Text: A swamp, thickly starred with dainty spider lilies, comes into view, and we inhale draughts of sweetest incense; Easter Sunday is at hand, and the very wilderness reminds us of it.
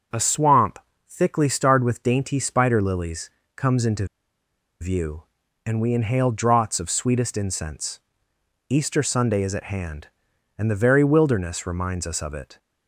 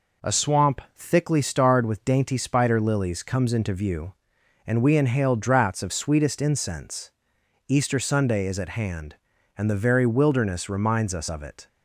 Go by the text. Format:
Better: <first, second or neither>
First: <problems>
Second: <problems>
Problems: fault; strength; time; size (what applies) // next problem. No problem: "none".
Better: second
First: pauses between "into" and "view"; noticeable; at 4.0 s; 0.75 s long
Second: none